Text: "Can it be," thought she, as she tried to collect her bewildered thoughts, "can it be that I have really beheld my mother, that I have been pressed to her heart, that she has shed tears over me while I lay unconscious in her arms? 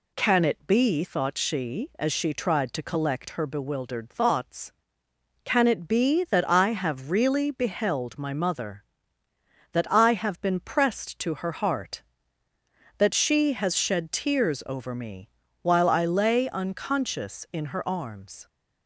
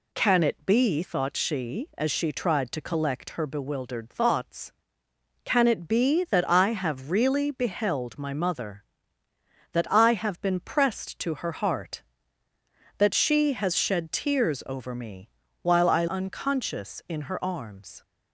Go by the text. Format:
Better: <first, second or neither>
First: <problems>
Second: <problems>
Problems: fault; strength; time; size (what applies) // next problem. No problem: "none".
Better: first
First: pauses between "me" and "while"; slight; at 15.2 s; 0.32 s long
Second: pauses between "me" and "while"; slight; at 15.2 s; 0.32 s long // skips "lay"; at 16.0 s